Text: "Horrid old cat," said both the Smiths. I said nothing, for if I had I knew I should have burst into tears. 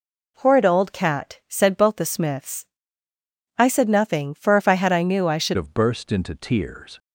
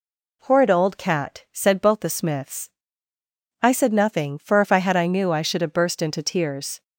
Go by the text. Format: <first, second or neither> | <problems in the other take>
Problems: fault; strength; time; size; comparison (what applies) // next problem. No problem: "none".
second | changes voice at "have"; from 5.5 s on; 1.4 s long